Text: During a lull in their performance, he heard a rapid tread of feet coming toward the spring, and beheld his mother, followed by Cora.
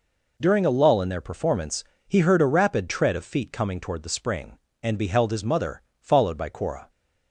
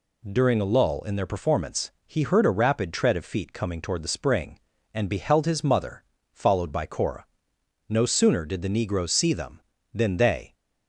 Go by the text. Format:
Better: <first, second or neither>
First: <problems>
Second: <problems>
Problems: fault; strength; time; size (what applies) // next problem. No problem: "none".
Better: first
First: none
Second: goes on to say "No sooner did the negroes see them than they"; strong; from 7.8 s on; 2.6 s long